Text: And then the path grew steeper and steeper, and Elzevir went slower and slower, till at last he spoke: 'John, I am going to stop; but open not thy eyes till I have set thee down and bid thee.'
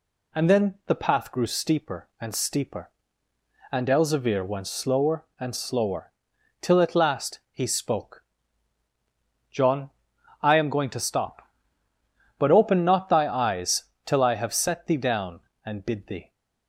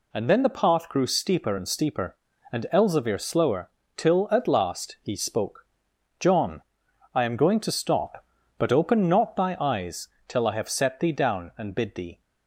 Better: first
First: pauses between "eyes" and "till"; slight; at 13.8 s; 0.20 s long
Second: skips "went slower and"; at 3.1 s // pauses between "eyes" and "till"; slight; at 10.0 s; 0.20 s long

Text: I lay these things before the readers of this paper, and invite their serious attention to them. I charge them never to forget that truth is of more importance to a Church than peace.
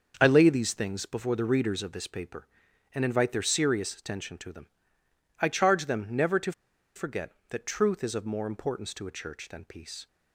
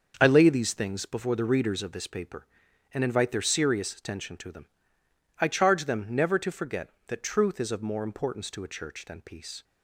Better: second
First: starts louder than the rest; until 1.2 s; 6.5 dB // pauses between "to" and "forget"; at 6.5 s; 0.42 s long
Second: starts louder than the rest; until 1.2 s; 6.5 dB

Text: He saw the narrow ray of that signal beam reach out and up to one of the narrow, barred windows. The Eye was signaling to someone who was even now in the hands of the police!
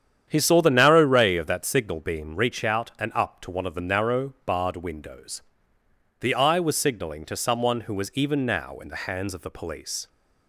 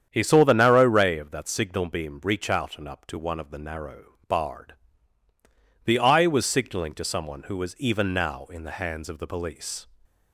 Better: first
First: starts louder than the rest; strong; until 1.2 s; 9 dB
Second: starts louder than the rest; strong; until 1.1 s; 8.5 dB // skips "windows"; at 5.2 s

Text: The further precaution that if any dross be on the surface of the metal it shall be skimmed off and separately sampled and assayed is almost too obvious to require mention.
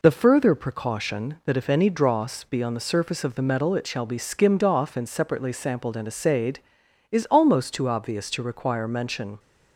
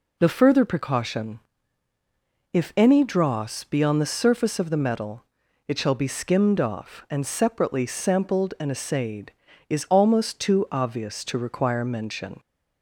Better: first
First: none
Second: skips "that"; at 1.9 s // pauses between "metal" and "it"; noticeable; at 5.2 s; 0.46 s long

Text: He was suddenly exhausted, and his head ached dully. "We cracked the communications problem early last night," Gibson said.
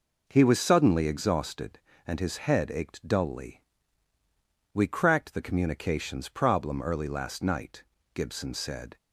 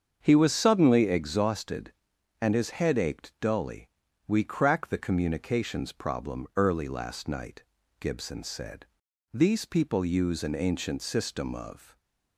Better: first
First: none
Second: starts louder than the rest; strong; until 1.2 s; 7 dB // goes on to say "These people use an ancient system of"; strong; from 9.3 s on; 2.6 s long

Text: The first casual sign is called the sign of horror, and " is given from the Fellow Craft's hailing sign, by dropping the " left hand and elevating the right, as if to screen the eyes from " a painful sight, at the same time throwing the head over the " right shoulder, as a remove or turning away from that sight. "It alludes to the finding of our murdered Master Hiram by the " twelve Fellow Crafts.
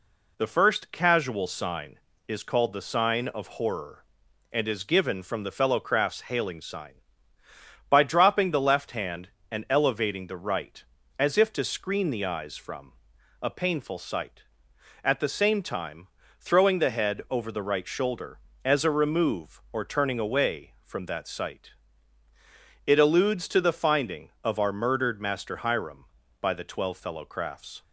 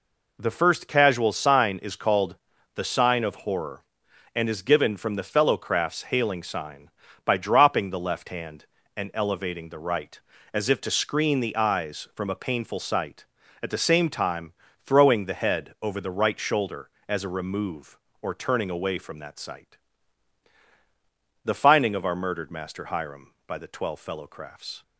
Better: first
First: pauses between "time" and "throwing"; slight; at 16.0 s; 0.32 s long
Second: pauses between "called" and "the"; at 2.3 s; 0.38 s long // pauses between "time" and "throwing"; slight; at 14.5 s; 0.32 s long // skips "It alludes to"; at 20.6 s

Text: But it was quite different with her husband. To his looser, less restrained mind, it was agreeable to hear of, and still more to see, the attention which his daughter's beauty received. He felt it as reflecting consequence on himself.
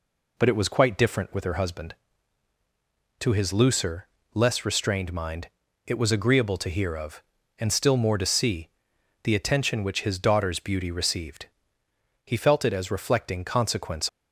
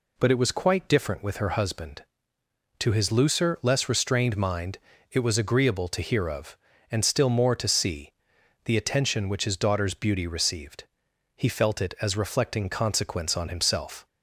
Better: second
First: stops before "on himself"; at 14.0 s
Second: none

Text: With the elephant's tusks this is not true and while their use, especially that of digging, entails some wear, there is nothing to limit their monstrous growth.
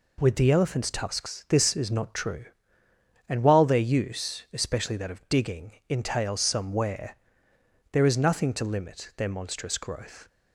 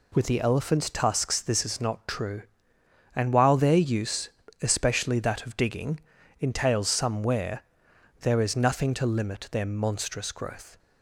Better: neither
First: none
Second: none

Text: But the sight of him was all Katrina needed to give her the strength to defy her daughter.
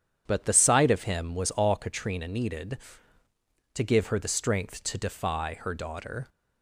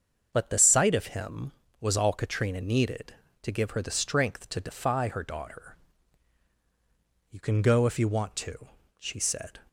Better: first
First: none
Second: starts louder than the rest; until 1.3 s; 7 dB // goes on to say "You can go if you want to she said"; strong; from 7.2 s on; 2.3 s long

